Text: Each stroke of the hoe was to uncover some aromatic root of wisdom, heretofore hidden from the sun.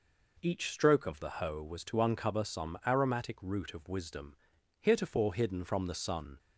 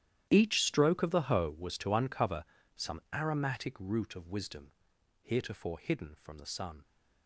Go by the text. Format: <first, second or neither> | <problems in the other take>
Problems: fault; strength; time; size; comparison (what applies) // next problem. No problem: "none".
first | gets quieter; strong; throughout; 18.5 dB // pauses between "uncover" and "some"; slight; at 2.4 s; 0.32 s long